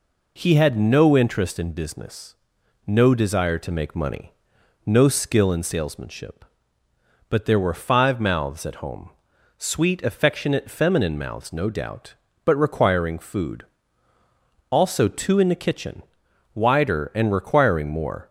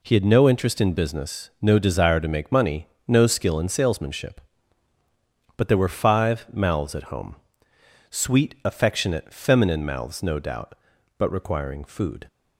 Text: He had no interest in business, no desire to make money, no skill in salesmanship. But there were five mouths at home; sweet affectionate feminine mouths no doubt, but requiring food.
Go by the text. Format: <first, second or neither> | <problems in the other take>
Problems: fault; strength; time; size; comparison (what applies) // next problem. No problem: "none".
second | goes on to say "Also two in the kitchen wider and requiring more"; strong; from 14.6 s on; 3.6 s long